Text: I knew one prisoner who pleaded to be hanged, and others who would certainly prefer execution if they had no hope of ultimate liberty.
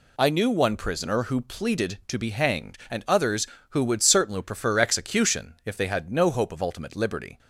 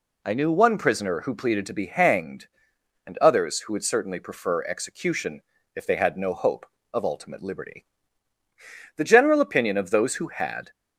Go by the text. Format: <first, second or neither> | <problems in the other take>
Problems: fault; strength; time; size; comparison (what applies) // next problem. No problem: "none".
first | pauses between "execution" and "if"; slight; at 5.4 s; 0.34 s long // goes on to say "The general opinion of those who had"; strong; from 8.9 s on; 1.7 s long